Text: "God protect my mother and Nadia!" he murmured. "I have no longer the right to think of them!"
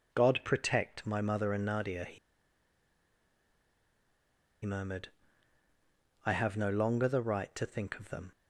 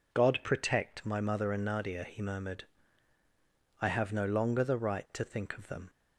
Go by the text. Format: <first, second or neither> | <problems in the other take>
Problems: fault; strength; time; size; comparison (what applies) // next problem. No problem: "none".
second | pauses between "he" and "murmured"; strong; at 2.1 s; 2.4 s long